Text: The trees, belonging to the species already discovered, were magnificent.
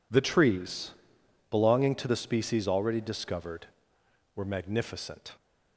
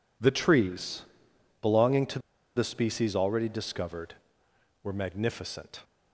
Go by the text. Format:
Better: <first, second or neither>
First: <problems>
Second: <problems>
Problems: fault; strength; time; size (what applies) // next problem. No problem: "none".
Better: first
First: none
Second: pauses between "to" and "the"; at 2.1 s; 0.37 s long